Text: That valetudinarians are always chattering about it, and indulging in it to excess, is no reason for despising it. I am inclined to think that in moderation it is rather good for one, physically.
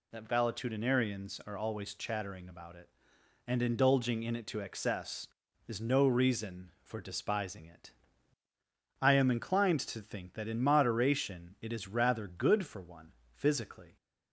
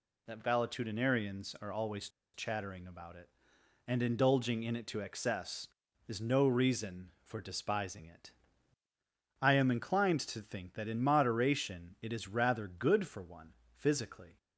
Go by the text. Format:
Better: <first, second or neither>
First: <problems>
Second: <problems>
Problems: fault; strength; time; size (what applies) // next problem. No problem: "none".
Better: first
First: none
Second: pauses between "always" and "chattering"; slight; at 2.0 s; 0.26 s long